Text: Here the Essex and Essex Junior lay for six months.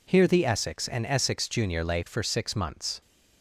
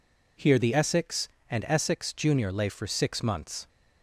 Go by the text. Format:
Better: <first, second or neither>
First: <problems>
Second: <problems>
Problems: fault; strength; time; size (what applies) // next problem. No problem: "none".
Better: neither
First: none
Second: none